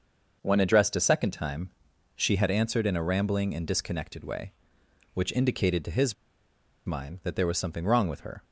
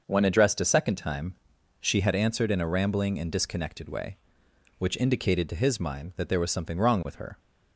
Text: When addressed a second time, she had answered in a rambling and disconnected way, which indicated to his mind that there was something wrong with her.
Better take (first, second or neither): second